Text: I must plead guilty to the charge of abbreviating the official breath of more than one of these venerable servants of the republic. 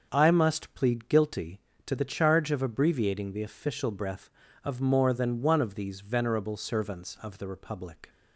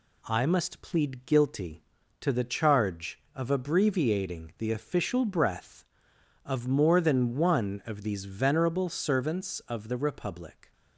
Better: neither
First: none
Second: none

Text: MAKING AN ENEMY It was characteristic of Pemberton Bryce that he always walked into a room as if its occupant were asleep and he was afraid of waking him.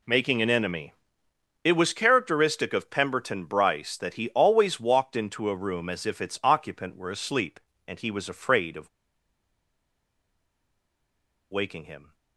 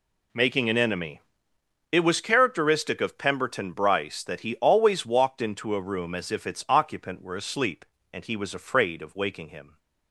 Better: second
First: pauses between "ENEMY" and "It"; noticeable; at 0.9 s; 0.70 s long // pauses between "of" and "waking"; strong; at 8.8 s; 2.6 s long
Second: pauses between "ENEMY" and "It"; noticeable; at 1.1 s; 0.70 s long

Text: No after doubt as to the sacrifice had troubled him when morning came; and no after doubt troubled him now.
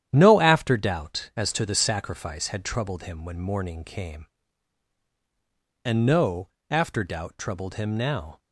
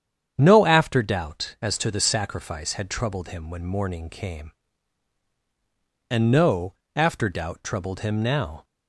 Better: second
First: gets quieter; throughout; 7 dB // starts louder than the rest; strong; until 1.1 s; 10.5 dB // pauses between "no" and "after"; slight; at 6.4 s; 0.22 s long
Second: starts louder than the rest; strong; until 1.3 s; 8.5 dB // pauses between "no" and "after"; slight; at 6.7 s; 0.22 s long

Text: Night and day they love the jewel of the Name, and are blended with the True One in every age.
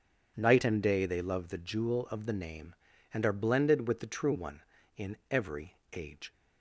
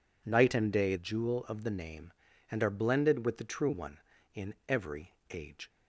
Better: first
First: pauses between "every" and "age"; slight; at 5.7 s; 0.16 s long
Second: skips "they love the"; at 0.9 s // pauses between "every" and "age"; slight; at 5.1 s; 0.16 s long

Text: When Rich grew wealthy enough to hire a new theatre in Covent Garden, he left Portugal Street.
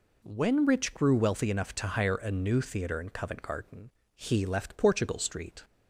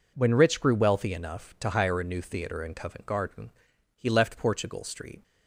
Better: neither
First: none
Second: none

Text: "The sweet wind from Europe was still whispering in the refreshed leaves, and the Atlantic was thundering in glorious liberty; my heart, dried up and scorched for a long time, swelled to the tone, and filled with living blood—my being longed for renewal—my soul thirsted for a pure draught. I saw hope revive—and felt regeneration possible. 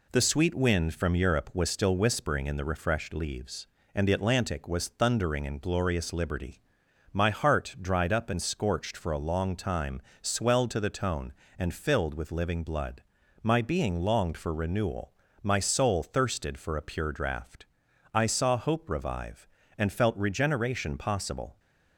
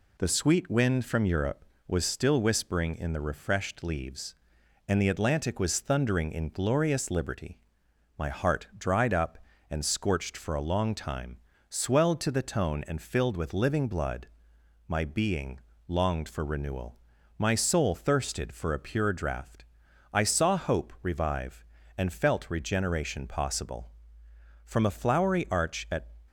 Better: first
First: none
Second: pauses between "being" and "longed"; slight; at 15.5 s; 0.30 s long // goes on to say "From a flowery arch at"; from 24.6 s on; 1.5 s long

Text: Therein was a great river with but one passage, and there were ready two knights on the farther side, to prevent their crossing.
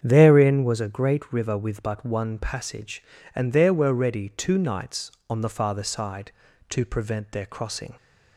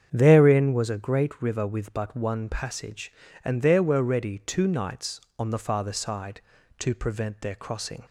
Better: neither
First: starts louder than the rest; strong; until 1.0 s; 8 dB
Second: starts louder than the rest; strong; until 1.1 s; 8 dB

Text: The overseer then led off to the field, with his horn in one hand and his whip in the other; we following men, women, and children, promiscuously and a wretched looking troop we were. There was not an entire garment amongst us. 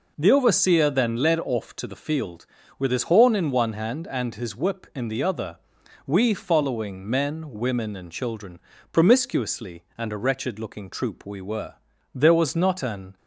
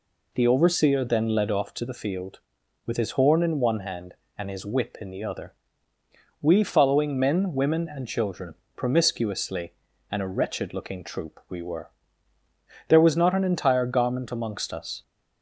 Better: second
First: stops before "entire garment amongst us"; at 13.1 s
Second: none

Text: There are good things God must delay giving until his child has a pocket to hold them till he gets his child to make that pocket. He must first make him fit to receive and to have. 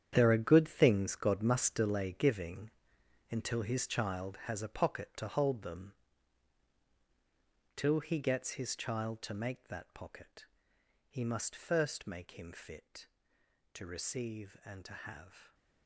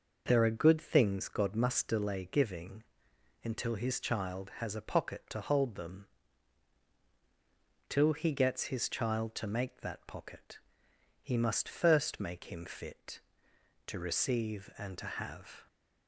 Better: second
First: gets quieter; strong; throughout; 13 dB // pauses between "giving" and "until"; noticeable; at 2.6 s; 0.62 s long // pauses between "them" and "till"; strong; at 5.9 s; 1.8 s long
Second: pauses between "giving" and "until"; noticeable; at 2.8 s; 0.62 s long // pauses between "them" and "till"; strong; at 6.0 s; 1.8 s long

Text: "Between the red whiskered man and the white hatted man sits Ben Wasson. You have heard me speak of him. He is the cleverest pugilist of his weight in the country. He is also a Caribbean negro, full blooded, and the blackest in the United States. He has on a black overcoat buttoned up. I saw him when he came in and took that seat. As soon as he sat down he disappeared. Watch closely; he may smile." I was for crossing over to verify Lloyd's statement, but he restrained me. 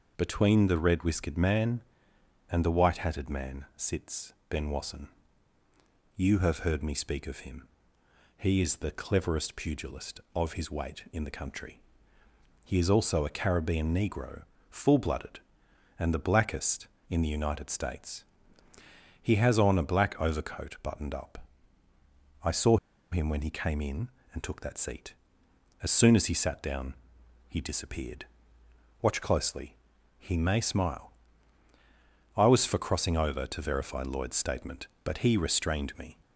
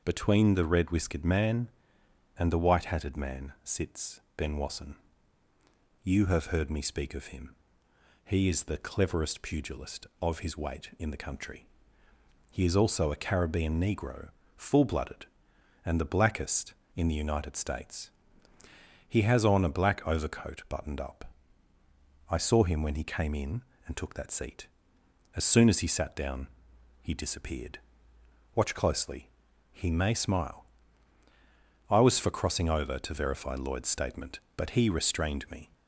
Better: second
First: pauses between "sits" and "Ben"; slight; at 4.3 s; 0.16 s long // pauses between "saw" and "him"; slight; at 22.7 s; 0.34 s long // pauses between "down" and "he"; noticeable; at 26.9 s; 0.54 s long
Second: pauses between "sits" and "Ben"; slight; at 4.2 s; 0.16 s long // pauses between "down" and "he"; noticeable; at 26.4 s; 0.54 s long

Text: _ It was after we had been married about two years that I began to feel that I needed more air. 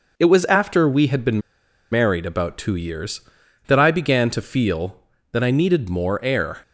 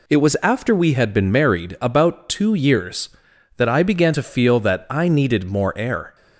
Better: second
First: pauses between "been" and "married"; noticeable; at 1.3 s; 0.52 s long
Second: none

